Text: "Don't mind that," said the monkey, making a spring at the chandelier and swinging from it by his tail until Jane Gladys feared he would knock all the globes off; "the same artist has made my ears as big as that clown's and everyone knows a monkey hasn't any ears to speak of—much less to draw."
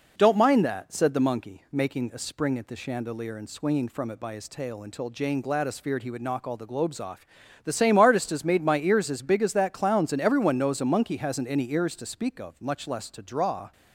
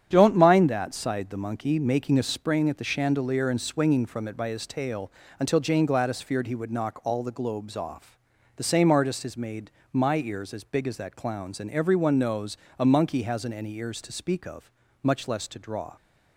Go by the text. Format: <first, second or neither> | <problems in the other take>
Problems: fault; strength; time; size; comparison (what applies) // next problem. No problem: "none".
first | starts louder than the rest; strong; until 1.1 s; 9 dB // says "sighed" for "said"; at 0.9 s // pauses between "tail" and "until"; slight; at 5.0 s; 0.30 s long // pauses between "made" and "my"; slight; at 9.6 s; 0.24 s long // pauses between "knows" and "a"; slight; at 12.5 s; 0.20 s long